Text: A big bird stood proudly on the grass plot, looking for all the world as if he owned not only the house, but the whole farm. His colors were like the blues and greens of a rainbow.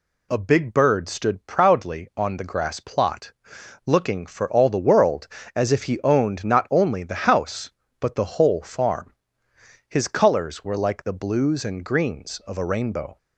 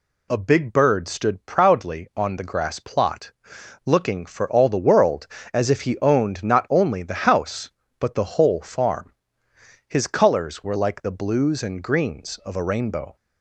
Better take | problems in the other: neither | none

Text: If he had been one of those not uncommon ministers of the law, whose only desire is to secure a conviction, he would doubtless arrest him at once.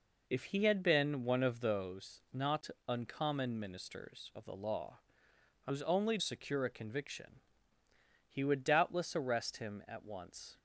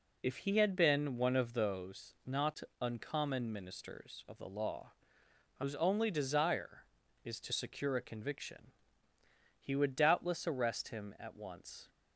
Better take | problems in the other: second | pauses between "not" and "uncommon"; slight; at 2.6 s; 0.20 s long; slight in the second // skips "desire is to"; at 6.1 s

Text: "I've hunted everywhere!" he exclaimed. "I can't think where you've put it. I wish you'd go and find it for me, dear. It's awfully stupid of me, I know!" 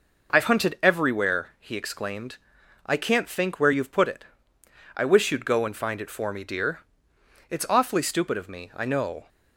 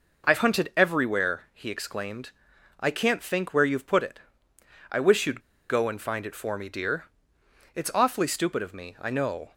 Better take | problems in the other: first | pauses between "you'd" and "go"; slight; at 5.4 s; 0.28 s long

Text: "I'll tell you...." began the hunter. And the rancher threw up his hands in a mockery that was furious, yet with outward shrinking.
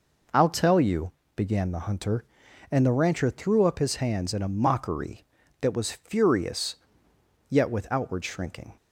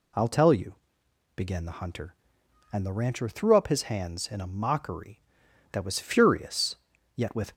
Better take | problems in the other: first | stops before "outward shrinking"; at 7.5 s

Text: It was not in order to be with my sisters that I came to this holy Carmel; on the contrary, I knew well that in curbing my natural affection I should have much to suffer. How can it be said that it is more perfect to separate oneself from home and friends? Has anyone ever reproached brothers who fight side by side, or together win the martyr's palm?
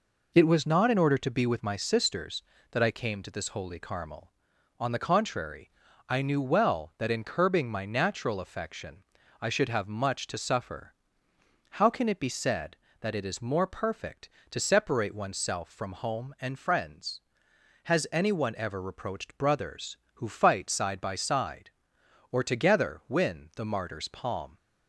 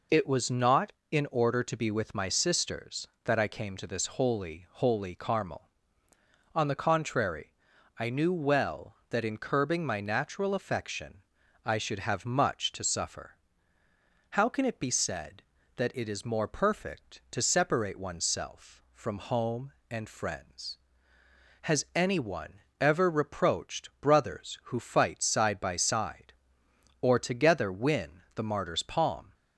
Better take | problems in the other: first | says "holy" twice; at 4.7 s // pauses between "affection" and "I"; at 11.2 s; 0.42 s long; also in the first // pauses between "anyone" and "ever"; slight; at 22.6 s; 0.20 s long

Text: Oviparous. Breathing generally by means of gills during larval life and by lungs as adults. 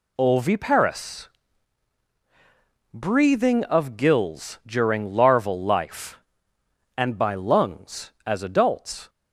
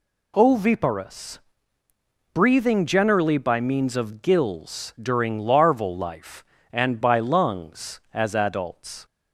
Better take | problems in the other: second | skips "generally by means"; at 3.6 s

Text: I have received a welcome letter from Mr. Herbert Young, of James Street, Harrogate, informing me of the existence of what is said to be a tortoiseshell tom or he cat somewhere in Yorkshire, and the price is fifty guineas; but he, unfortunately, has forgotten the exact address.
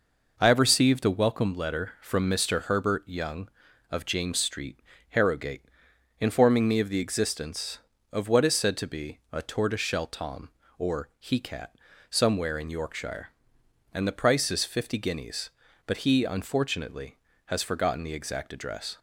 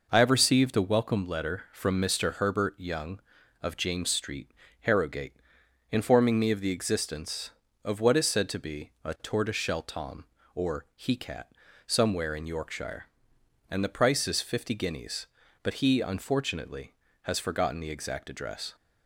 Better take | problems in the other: neither | pauses between "cat" and "somewhere"; slight; the same in both

